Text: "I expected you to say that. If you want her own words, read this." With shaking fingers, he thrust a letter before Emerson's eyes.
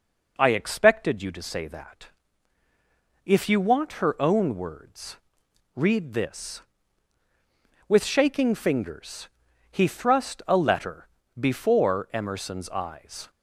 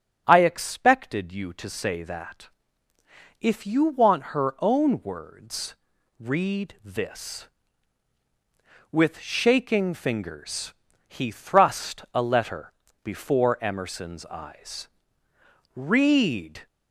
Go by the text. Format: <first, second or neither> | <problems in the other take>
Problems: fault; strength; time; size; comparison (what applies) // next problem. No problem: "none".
first | starts louder than the rest; strong; until 1.2 s; 9 dB // pauses between "letter" and "before"; at 12.7 s; 0.38 s long; slight in the first // goes on to say "Read"; noticeable; from 15.7 s on; 0.90 s long